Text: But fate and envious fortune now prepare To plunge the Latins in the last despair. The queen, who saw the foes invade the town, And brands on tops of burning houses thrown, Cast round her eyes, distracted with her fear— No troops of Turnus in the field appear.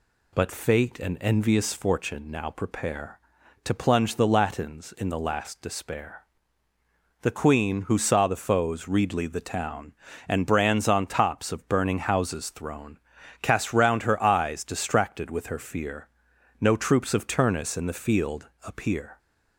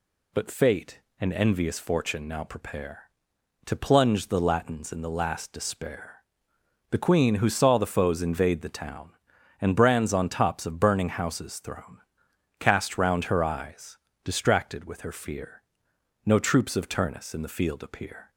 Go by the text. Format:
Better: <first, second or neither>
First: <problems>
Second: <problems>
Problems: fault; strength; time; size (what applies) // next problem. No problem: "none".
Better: second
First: says "readly" for "invade"; at 8.8 s // pauses between "field" and "appear"; slight; at 18.4 s; 0.16 s long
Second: none